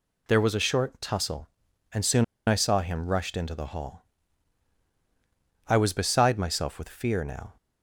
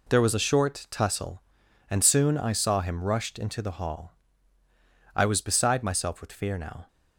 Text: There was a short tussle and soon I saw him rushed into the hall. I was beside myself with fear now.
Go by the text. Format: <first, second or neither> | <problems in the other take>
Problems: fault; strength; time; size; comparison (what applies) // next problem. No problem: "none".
second | pauses between "soon" and "I"; slight; at 2.2 s; 0.23 s long